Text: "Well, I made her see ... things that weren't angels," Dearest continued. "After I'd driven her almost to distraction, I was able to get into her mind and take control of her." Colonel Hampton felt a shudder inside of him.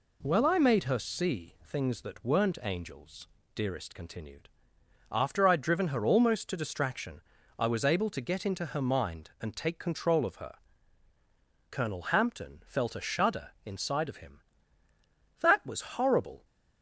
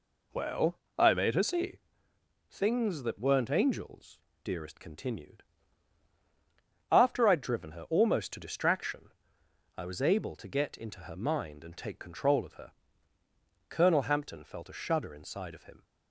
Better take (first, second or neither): second